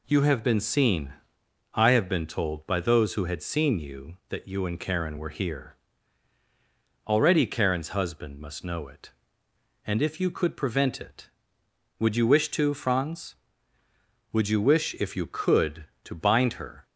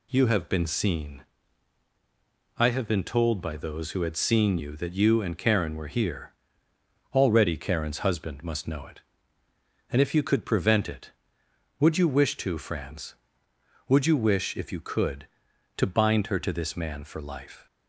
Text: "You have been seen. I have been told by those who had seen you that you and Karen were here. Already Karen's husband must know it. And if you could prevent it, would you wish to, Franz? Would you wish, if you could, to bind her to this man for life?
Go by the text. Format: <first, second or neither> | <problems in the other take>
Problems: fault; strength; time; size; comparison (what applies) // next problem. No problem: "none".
second | stops before "to this man for life"; at 16.8 s